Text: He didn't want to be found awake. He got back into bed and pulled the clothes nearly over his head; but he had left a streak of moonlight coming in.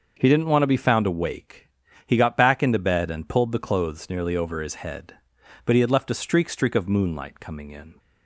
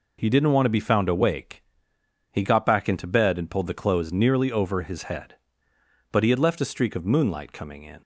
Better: second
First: starts louder than the rest; noticeable; until 1.2 s; 6 dB // says "streak" twice; at 6.4 s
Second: none

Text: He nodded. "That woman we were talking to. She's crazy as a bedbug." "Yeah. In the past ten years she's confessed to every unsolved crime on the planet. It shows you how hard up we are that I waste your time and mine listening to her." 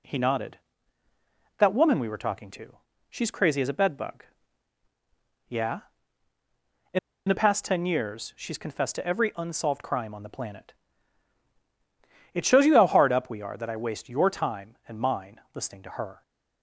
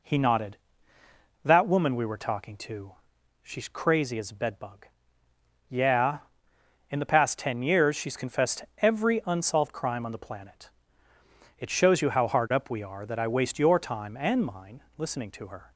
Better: second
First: pauses between "In" and "the"; slight; at 6.9 s; 0.28 s long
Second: none

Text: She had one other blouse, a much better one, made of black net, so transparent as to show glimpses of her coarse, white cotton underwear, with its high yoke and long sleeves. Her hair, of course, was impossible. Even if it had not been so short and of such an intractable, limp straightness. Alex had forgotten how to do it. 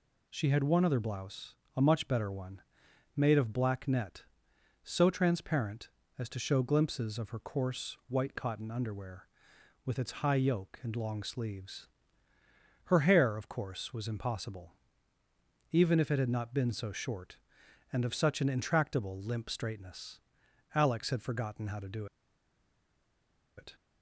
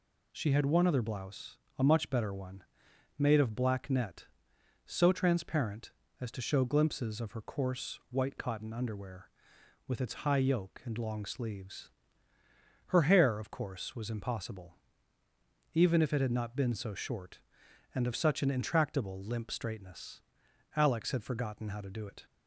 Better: second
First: pauses between "do" and "it"; strong; at 22.0 s; 1.5 s long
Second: none

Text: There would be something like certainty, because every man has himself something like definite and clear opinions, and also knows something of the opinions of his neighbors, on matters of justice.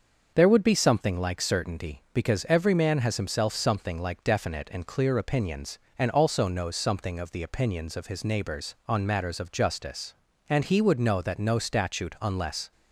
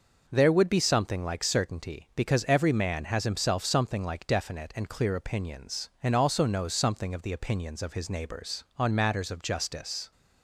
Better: second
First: starts louder than the rest; until 1.3 s; 6.5 dB // goes on to say "And he would know that no statute unless"; strong; from 10.4 s on; 2.2 s long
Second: none

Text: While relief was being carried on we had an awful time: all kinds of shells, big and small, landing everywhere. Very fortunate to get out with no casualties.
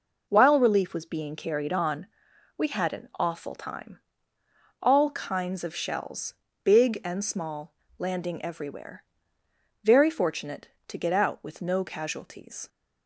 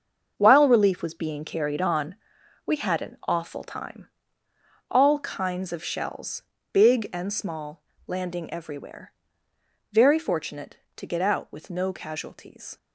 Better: first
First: pauses between "on" and "we"; noticeable; at 2.0 s; 0.52 s long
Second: gets quieter; strong; throughout; 10 dB // pauses between "on" and "we"; noticeable; at 2.1 s; 0.52 s long

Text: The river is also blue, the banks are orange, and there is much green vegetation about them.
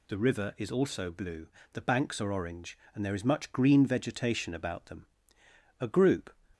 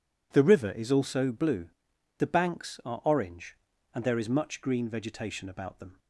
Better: second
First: goes on to say "A group"; from 5.7 s on; 0.52 s long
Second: none

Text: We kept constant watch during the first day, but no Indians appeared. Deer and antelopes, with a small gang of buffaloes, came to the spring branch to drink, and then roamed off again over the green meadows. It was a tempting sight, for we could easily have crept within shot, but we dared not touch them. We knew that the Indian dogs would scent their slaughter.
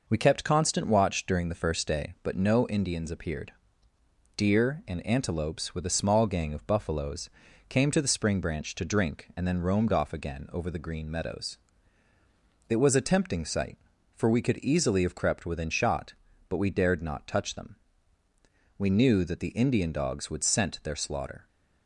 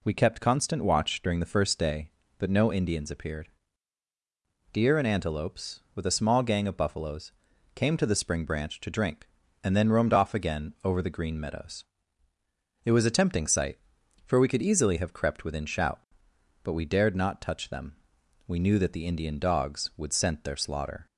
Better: first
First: none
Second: says "shout" for "shot"; at 15.6 s

